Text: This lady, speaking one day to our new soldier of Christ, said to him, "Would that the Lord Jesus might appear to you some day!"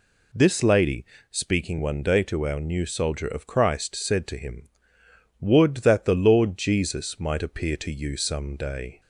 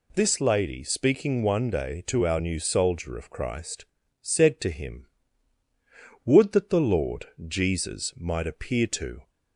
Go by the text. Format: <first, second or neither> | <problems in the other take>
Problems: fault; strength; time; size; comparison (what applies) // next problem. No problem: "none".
first | pauses between "Lord" and "Jesus"; slight; at 7.2 s; 0.20 s long // stops before "you some day"; at 9.2 s